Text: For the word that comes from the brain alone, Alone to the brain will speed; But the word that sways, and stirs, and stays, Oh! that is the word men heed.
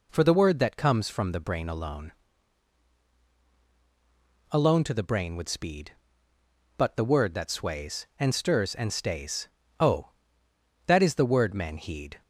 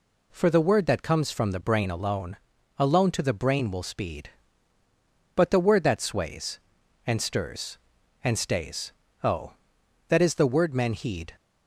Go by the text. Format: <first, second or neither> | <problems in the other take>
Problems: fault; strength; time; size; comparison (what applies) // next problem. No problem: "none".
second | says "would" for "will"; at 5.3 s